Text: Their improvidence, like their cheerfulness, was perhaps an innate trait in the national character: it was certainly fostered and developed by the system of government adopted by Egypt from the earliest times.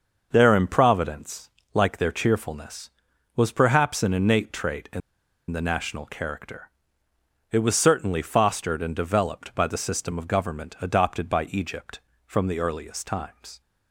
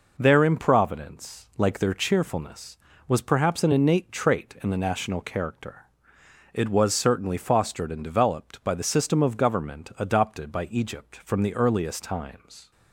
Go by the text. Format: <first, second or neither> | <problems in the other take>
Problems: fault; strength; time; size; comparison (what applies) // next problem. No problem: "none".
second | starts louder than the rest; noticeable; until 1.3 s; 6 dB // pauses between "in" and "the"; noticeable; at 5.0 s; 0.49 s long